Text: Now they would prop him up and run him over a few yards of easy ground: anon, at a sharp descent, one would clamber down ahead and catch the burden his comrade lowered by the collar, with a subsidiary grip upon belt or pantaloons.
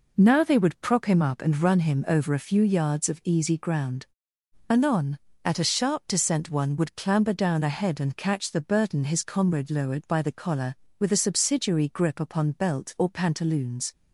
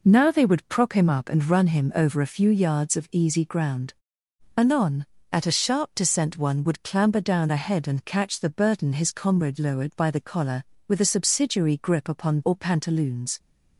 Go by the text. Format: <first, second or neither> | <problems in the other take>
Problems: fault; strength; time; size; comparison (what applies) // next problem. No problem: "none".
first | skips "belt"; at 12.4 s